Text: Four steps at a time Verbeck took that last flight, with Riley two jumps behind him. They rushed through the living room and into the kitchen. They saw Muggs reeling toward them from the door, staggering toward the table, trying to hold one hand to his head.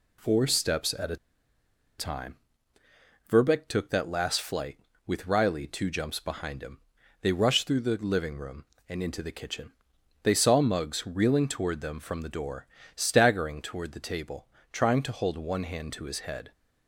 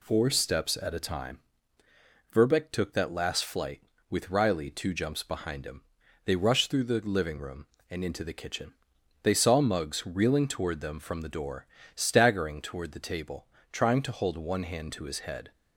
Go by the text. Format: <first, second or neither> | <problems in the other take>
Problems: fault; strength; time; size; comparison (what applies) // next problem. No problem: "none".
second | pauses between "a" and "time"; noticeable; at 1.1 s; 0.82 s long // pauses between "time" and "Verbeck"; noticeable; at 2.3 s; 0.94 s long; noticeable in the second